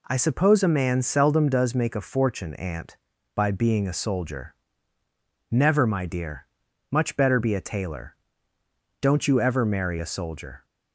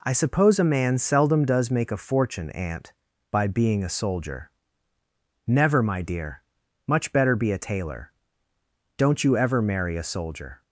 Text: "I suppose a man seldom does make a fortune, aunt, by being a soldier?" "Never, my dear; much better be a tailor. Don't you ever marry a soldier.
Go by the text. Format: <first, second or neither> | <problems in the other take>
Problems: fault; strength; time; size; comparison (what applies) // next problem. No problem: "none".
neither | none